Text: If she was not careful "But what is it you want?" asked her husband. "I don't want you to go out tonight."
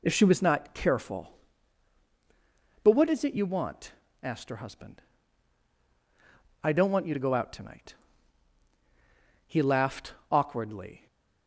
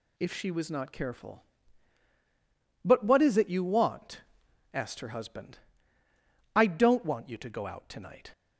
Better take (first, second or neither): second